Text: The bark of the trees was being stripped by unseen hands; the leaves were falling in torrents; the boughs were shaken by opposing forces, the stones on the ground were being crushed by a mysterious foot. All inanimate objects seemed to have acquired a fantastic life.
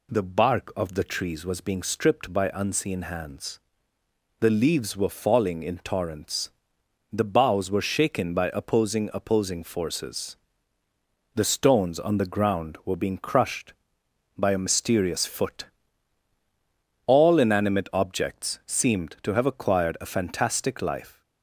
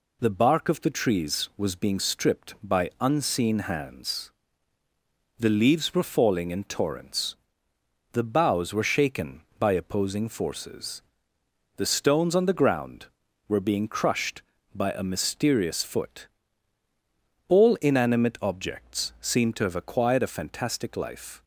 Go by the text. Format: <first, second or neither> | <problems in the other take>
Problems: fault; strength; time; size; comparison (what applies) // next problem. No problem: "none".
second | says "opposing" twice; at 9.1 s